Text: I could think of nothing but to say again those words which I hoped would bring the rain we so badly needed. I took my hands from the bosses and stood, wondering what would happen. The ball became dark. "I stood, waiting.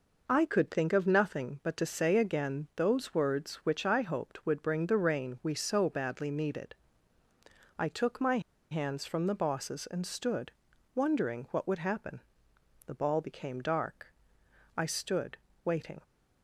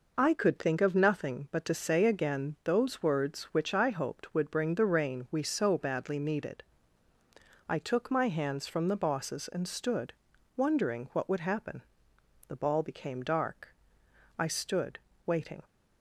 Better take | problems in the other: second | pauses between "my" and "hands"; slight; at 8.3 s; 0.31 s long

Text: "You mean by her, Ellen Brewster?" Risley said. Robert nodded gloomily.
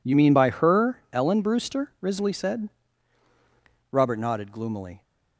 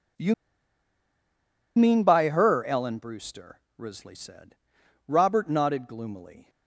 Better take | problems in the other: first | pauses between "You" and "mean"; strong; at 0.3 s; 1.4 s long

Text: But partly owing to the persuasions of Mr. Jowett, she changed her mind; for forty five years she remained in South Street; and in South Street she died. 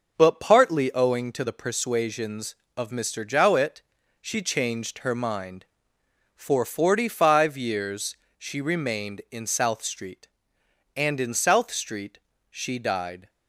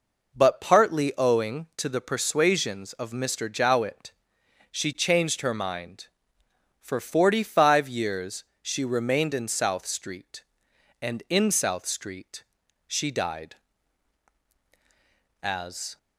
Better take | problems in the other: first | pauses between "years" and "she"; slight; at 8.4 s; 0.20 s long; slight in the first // pauses between "Street" and "she"; noticeable; at 12.4 s; 0.46 s long; slight in the first // goes on to say "As"; from 15.4 s on; 0.54 s long

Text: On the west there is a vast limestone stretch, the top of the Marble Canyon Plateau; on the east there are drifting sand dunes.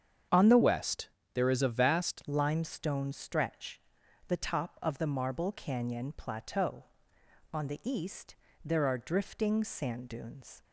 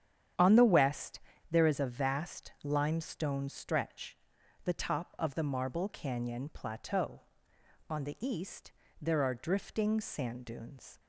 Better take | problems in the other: second | starts louder than the rest; strong; until 1.6 s; 8 dB; strong in the second // changes voice from "west" to "vast"; from 0.6 to 2.2 s; 1.6 s long // pauses between "west" and "there"; slight; at 1.0 s; 0.28 s long; slight in the second // pauses between "east" and "there"; slight; at 8.3 s; 0.32 s long; slight in the second

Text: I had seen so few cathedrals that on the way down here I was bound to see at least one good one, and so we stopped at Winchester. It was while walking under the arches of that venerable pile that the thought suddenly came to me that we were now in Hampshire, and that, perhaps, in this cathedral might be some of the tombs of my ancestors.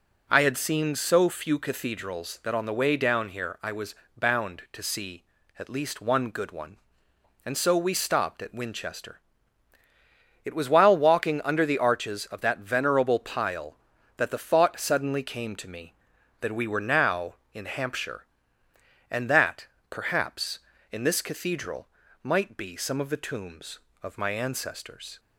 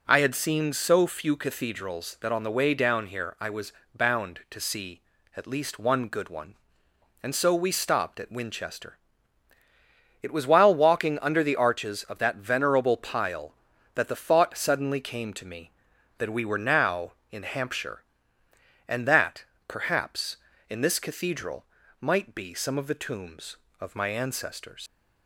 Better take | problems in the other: first | pauses between "was" and "bound"; slight; at 3.7 s; 0.22 s long; slight in the first // pauses between "cathedral" and "might"; slight; at 21.6 s; 0.34 s long; slight in the first // leaves "ancestors" unfinished; at 24.8 s; 110 ms

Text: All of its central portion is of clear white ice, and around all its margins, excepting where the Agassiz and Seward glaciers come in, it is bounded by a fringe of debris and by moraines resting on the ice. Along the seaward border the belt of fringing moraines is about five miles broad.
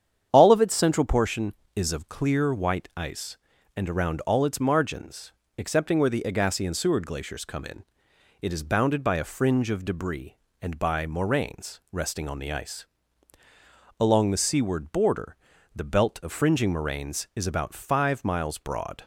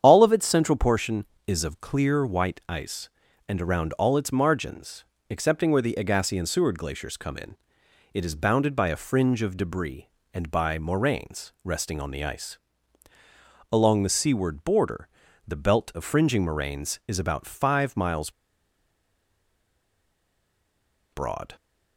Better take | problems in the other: first | starts louder than the rest; strong; until 1.0 s; 8.5 dB; strong in the first // pauses between "border" and "the"; at 15.0 s; 0.40 s long; also in the first // pauses between "miles" and "broad"; strong; at 18.3 s; 2.8 s long

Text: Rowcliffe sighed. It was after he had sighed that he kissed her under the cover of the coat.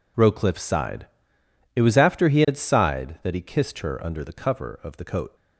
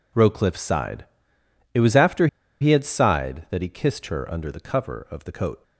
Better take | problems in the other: first | pauses between "after" and "he"; slight; at 2.2 s; 0.34 s long

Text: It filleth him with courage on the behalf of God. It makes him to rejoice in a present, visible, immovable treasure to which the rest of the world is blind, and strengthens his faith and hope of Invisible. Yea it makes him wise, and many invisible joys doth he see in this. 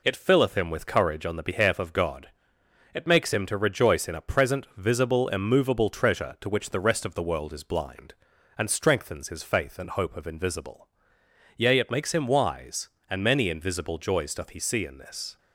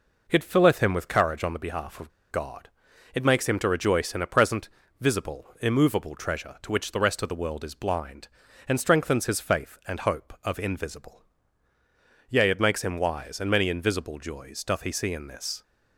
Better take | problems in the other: first | pauses between "of" and "God"; slight; at 2.1 s; 0.21 s long

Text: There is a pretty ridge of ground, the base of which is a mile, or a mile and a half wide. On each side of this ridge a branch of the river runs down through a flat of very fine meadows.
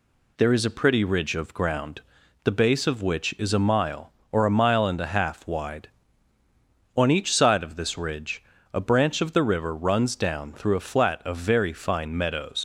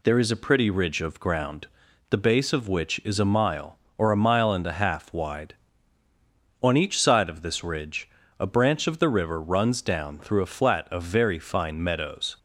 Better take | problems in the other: second | pauses between "ridge" and "a"; slight; at 8.4 s; 0.32 s long; slight in the second // leaves "meadows" unfinished; at 12.5 s; 80 ms

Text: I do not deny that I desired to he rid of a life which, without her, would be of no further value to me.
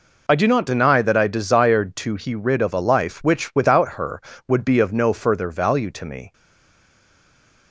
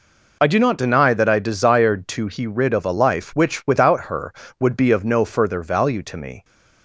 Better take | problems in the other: second | stays silent after the last word; noticeable; from 6.3 s on; 1.4 s long

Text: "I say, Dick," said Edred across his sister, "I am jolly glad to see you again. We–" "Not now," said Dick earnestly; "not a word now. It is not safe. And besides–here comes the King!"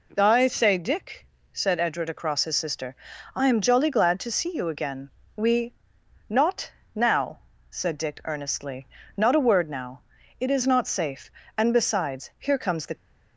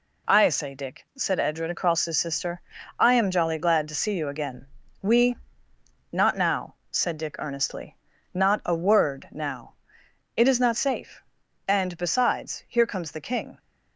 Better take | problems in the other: second | pauses between "Not" and "now"; slight; at 6.6 s; 0.28 s long // stops before "King"; at 12.9 s

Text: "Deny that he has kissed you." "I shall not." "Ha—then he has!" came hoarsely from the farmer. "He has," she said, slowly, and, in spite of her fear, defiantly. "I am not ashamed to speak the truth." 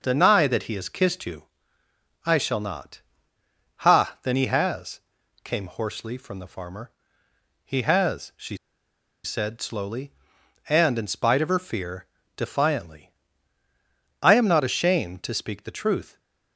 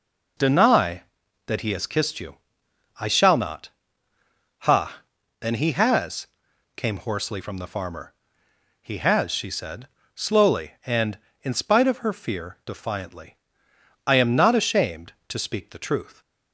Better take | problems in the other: second | starts louder than the rest; noticeable; until 1.0 s; 6 dB // pauses between "she" and "said"; noticeable; at 8.5 s; 0.68 s long

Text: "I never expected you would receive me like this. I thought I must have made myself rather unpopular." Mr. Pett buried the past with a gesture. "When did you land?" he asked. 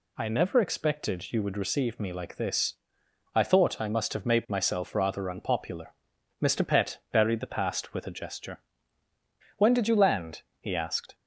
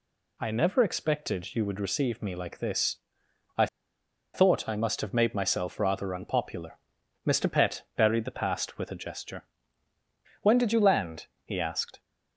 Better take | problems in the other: first | pauses between "I" and "thought"; noticeable; at 3.6 s; 0.67 s long // pauses between "Pett" and "buried"; slight; at 7.8 s; 0.16 s long; slight in the first

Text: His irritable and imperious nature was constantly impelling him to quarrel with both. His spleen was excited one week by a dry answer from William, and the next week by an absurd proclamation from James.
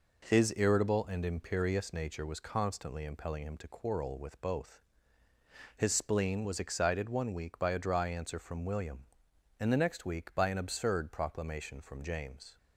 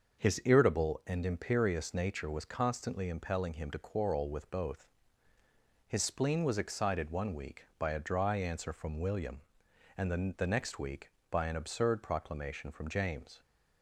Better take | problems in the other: first | starts louder than the rest; until 1.2 s; 6 dB // says "the" twice; at 10.3 s

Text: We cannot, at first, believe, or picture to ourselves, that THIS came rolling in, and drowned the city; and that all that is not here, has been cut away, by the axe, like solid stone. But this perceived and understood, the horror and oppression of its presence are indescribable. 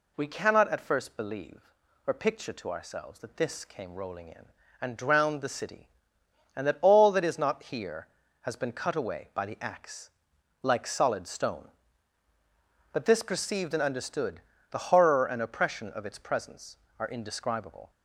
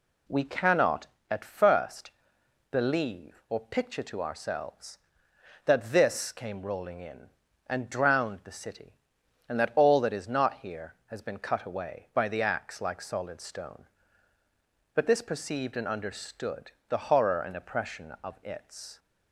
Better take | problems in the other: first | stops before "presence are indescribable"; at 18.9 s

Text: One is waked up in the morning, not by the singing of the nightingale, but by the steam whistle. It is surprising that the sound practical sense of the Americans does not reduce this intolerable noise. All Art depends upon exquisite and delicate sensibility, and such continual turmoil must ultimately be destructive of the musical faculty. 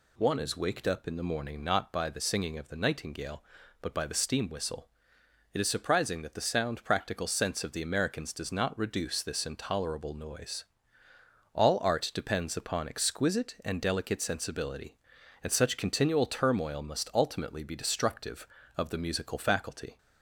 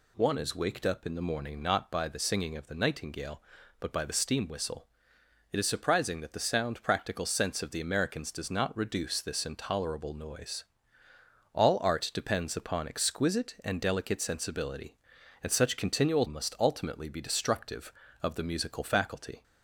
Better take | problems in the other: first | skips "turmoil"; at 16.2 s

